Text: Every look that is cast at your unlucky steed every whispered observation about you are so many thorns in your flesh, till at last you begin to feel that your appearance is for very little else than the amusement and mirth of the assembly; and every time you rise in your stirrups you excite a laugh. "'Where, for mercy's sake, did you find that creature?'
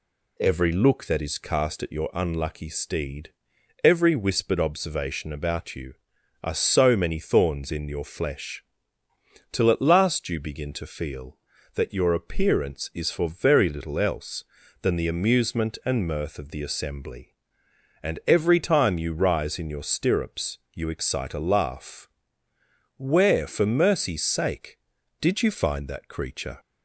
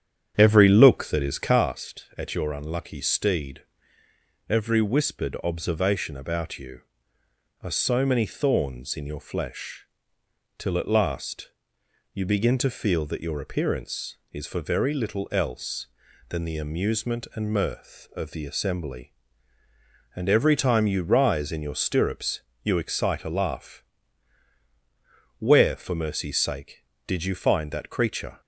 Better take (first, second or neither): first